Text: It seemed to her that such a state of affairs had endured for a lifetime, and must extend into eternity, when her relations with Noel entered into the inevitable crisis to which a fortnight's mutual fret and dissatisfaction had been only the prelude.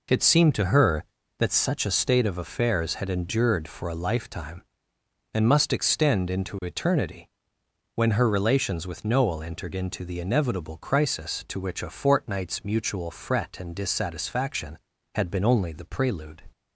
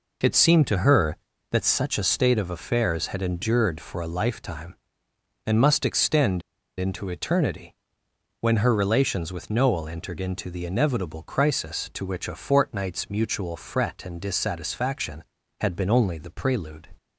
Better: first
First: none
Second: pauses between "extend" and "into"; at 6.4 s; 0.38 s long

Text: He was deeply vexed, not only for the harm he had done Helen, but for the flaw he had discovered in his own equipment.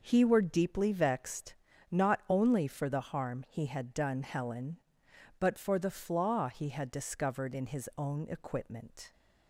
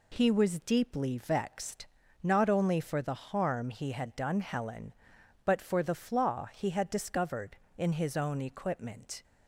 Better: second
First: says "were" for "was"; at 0.2 s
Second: none

